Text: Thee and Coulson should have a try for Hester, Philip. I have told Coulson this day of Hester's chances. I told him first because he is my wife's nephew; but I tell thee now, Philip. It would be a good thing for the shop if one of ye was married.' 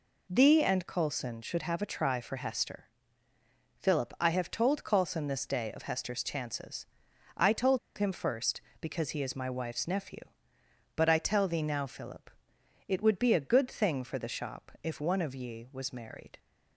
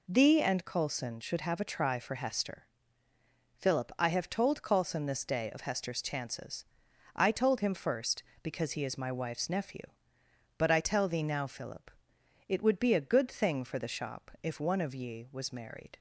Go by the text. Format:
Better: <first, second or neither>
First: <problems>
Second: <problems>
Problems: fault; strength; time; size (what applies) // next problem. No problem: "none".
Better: second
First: pauses between "told" and "him"; slight; at 7.7 s; 0.19 s long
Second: none